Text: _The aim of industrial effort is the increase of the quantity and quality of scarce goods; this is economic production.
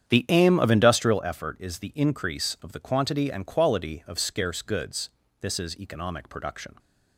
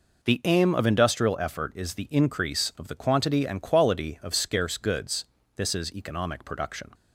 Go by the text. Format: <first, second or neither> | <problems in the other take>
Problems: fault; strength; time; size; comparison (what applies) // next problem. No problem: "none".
second | starts louder than the rest; strong; until 1.3 s; 9 dB